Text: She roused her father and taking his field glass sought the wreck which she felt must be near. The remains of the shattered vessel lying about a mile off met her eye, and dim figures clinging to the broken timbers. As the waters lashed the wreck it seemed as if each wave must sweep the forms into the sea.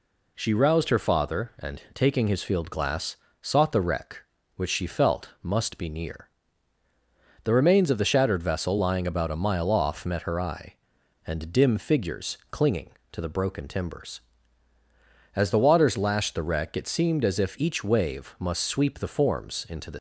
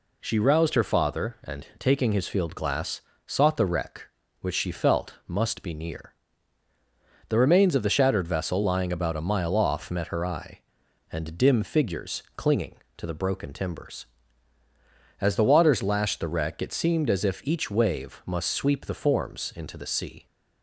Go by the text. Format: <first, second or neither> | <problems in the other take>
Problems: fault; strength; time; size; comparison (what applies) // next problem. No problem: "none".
second | pauses between "glass" and "sought"; slight; at 3.1 s; 0.26 s long; slight in the second // stops before "sea"; at 19.9 s